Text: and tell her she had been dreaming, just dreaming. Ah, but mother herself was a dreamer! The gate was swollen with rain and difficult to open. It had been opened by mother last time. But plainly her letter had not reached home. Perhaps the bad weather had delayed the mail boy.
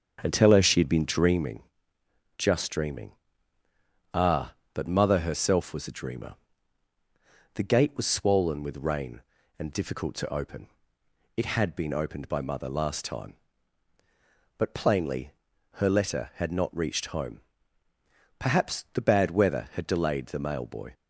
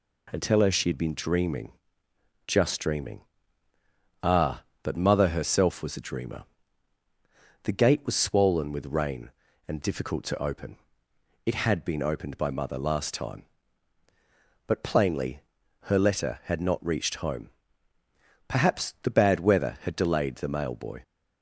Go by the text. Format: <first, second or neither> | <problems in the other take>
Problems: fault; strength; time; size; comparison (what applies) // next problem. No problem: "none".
second | starts louder than the rest; until 1.5 s; 7 dB // pauses between "plainly" and "her"; at 15.3 s; 0.42 s long; also in the second